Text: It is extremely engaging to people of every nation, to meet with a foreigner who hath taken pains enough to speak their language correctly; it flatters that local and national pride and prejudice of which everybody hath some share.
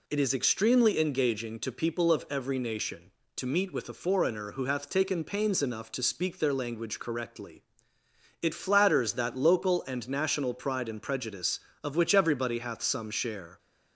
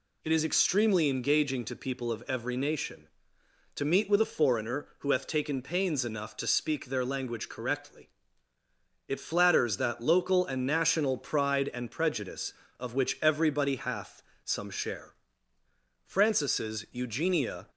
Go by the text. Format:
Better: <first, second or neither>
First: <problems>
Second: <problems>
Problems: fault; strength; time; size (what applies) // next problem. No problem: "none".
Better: first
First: none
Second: pauses between "hath" and "some"; slight; at 14.2 s; 0.24 s long // goes on to say "Francis's Eugenia"; from 16.0 s on; 1.6 s long